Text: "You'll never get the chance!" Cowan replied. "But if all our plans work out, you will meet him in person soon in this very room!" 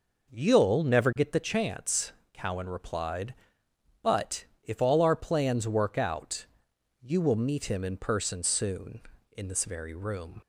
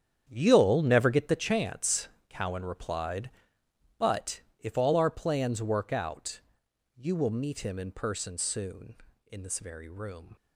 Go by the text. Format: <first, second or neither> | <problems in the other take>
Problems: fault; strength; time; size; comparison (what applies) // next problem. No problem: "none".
first | gets quieter; strong; throughout; 13 dB // pauses between "But" and "if"; slight; at 4.4 s; 0.18 s long; slight in the first